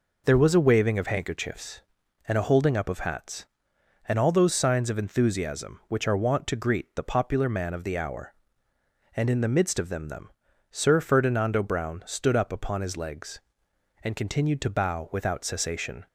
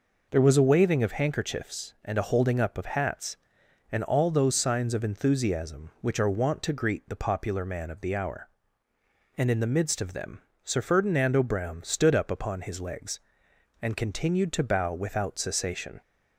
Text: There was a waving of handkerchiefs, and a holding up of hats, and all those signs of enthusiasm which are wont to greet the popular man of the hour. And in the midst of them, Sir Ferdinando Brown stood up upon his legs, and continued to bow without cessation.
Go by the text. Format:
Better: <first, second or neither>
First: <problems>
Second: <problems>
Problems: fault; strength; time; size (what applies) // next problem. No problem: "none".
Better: second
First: says "them" twice; at 10.0 s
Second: none